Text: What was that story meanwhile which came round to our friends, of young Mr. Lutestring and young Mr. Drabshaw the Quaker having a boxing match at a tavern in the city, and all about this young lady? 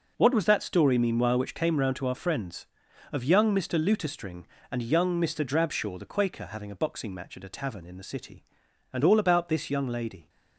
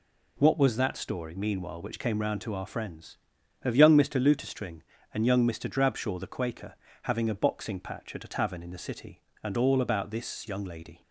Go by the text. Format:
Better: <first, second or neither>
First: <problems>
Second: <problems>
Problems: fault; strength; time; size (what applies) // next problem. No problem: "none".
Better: first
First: none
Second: pauses between "Quaker" and "having"; slight; at 6.7 s; 0.28 s long // says "patch" for "match"; at 7.7 s